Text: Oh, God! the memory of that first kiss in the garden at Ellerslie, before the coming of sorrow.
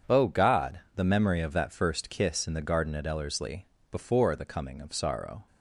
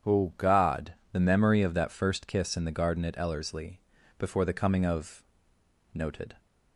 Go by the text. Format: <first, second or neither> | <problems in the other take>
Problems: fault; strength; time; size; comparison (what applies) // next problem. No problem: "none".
first | starts louder than the rest; strong; until 1.3 s; 8.5 dB // says "noted" for "sorrow"; at 5.9 s